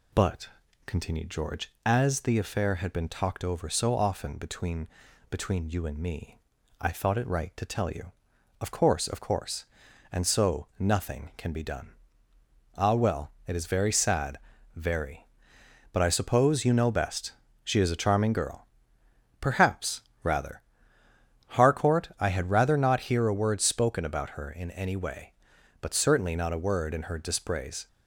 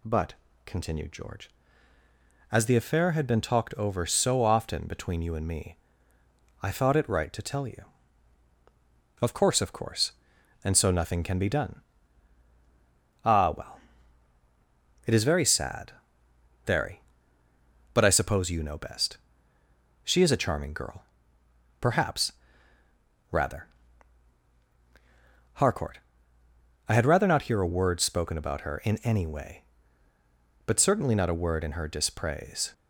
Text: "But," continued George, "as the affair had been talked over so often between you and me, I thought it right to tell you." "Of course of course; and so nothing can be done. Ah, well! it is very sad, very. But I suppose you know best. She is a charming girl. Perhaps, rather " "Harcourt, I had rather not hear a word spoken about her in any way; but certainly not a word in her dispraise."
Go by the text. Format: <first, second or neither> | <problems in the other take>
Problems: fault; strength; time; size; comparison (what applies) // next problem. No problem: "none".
second | says "between" twice; at 5.3 s